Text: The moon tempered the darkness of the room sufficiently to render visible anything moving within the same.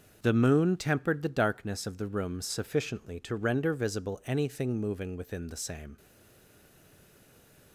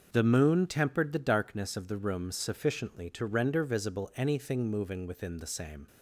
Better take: second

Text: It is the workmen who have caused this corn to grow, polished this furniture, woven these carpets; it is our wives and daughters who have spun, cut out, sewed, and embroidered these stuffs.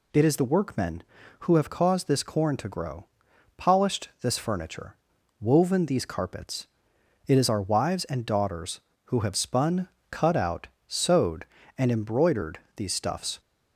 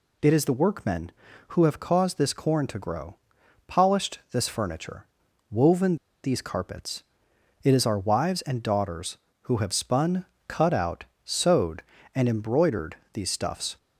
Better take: first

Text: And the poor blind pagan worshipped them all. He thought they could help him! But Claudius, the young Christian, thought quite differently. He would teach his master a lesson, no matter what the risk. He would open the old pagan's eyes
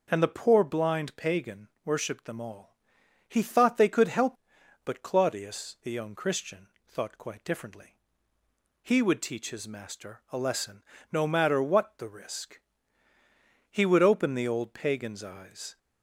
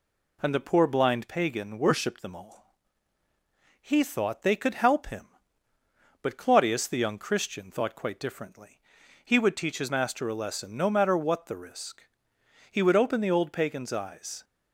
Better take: second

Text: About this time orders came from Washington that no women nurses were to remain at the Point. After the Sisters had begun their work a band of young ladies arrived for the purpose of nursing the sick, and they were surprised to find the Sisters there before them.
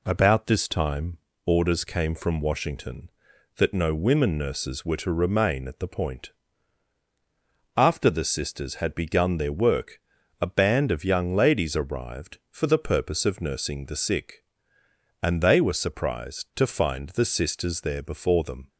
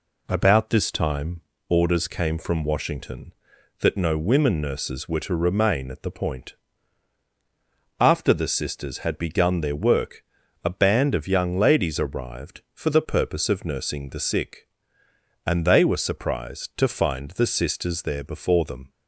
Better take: neither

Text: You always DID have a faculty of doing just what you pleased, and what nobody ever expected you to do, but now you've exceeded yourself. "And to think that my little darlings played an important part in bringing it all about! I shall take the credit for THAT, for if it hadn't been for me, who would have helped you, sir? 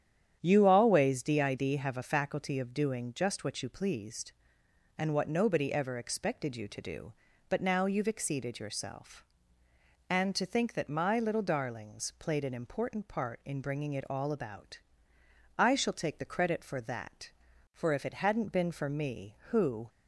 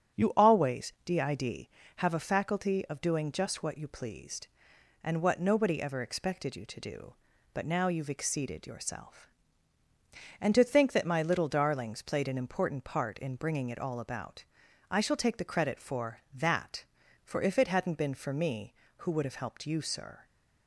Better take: second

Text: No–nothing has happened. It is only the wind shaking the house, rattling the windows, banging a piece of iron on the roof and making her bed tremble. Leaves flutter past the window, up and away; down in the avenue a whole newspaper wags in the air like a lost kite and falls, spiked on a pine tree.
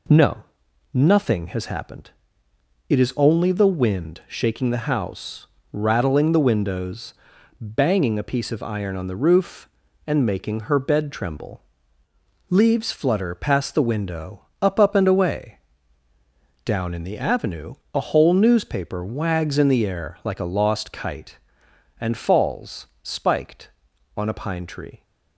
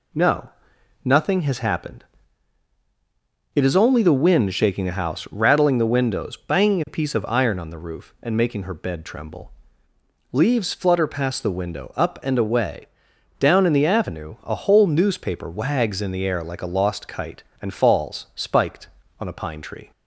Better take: second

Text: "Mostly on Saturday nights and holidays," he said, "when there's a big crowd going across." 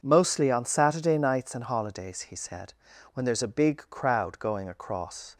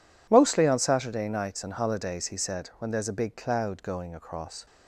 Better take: first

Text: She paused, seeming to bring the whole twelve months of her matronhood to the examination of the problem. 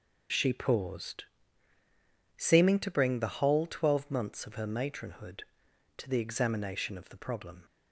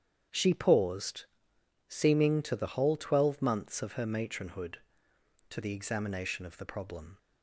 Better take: first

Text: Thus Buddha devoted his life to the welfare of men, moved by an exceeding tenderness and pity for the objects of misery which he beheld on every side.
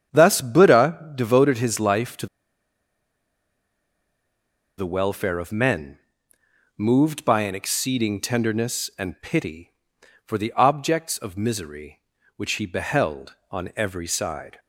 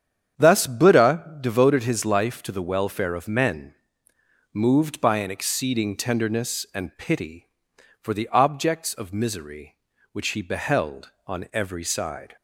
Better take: second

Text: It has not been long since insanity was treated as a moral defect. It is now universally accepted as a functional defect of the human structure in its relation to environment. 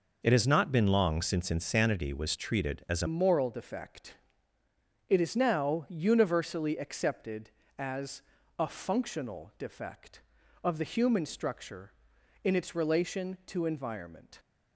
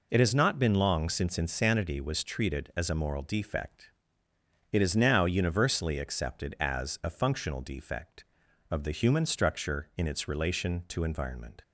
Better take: second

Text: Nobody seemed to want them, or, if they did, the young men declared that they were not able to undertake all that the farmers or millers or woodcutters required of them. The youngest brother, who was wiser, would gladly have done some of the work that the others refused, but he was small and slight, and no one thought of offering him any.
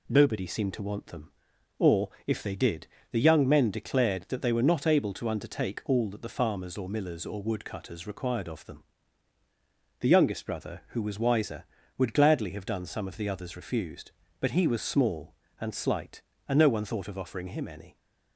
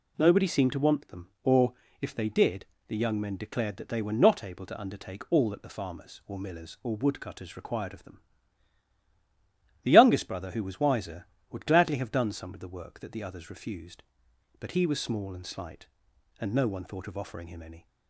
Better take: second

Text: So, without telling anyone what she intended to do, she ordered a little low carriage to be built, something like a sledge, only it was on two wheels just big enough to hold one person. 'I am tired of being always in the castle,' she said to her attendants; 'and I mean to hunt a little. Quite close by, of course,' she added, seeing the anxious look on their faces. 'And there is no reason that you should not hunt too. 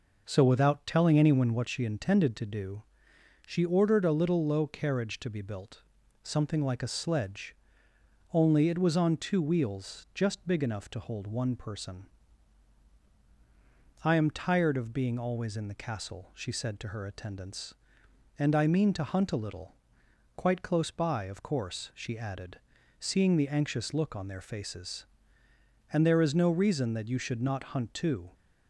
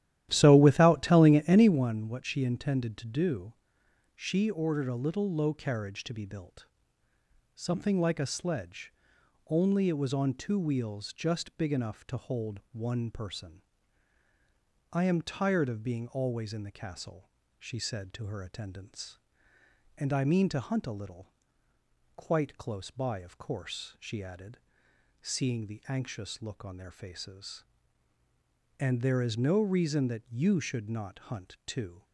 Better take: first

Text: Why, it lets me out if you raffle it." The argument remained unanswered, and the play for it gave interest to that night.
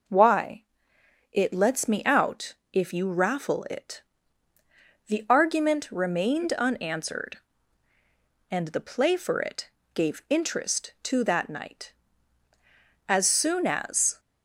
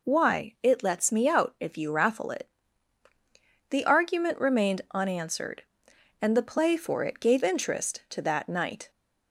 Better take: second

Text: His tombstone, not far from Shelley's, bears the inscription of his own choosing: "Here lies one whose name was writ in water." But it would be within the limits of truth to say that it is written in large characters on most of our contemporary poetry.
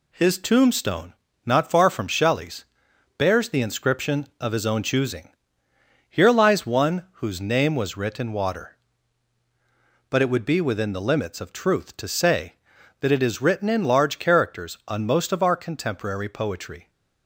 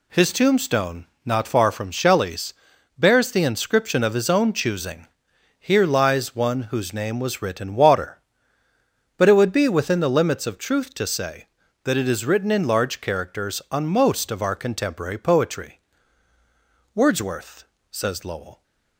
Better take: first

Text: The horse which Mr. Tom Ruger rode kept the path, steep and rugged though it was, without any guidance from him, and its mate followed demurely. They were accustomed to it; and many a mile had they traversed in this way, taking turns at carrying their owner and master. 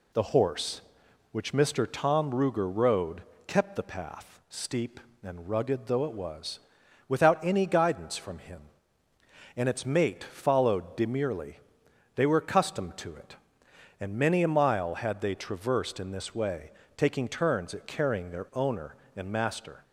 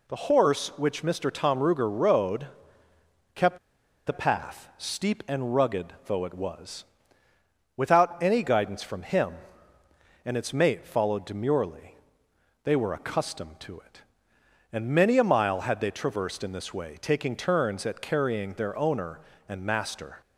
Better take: first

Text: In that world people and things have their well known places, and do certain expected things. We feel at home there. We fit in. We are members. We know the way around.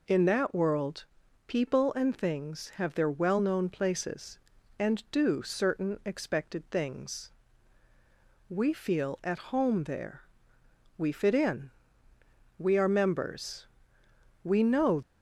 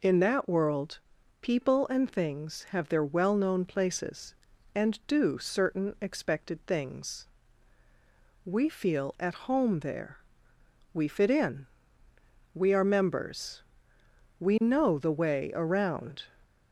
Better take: second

